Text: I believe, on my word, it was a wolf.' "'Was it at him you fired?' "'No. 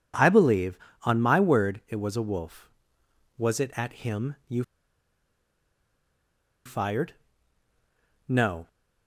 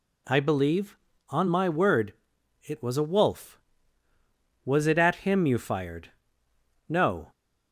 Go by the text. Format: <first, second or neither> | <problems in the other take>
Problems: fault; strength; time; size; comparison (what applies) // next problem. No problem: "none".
second | pauses between "you" and "fired"; strong; at 4.6 s; 2.0 s long